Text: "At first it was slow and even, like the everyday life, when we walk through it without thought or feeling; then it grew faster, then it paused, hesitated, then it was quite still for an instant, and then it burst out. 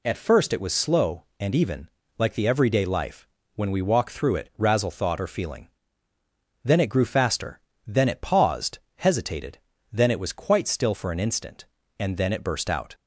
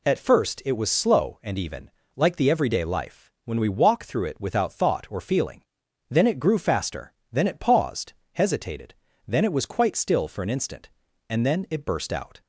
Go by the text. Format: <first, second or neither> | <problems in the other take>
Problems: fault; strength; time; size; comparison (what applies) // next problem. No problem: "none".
second | says "razzle" for "without"; at 4.5 s